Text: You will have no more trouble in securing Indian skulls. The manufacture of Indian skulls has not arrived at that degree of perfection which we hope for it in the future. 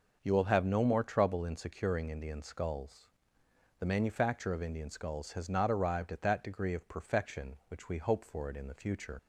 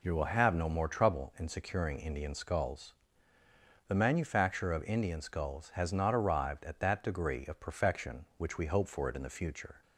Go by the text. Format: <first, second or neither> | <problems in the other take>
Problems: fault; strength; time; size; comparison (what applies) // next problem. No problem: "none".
second | leaves "future" unfinished; at 9.1 s; 55 ms